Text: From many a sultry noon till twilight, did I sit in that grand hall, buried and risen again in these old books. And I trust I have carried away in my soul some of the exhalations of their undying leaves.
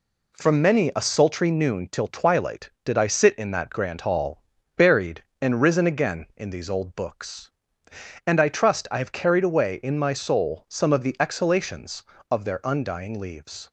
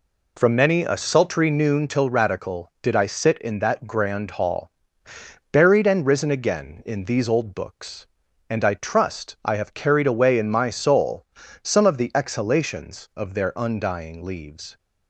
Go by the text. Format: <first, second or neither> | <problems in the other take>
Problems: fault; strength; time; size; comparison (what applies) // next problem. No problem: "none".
first | says "radical" for "twilight"; at 2.1 s // pauses between "soul" and "some"; at 11.2 s; 0.38 s long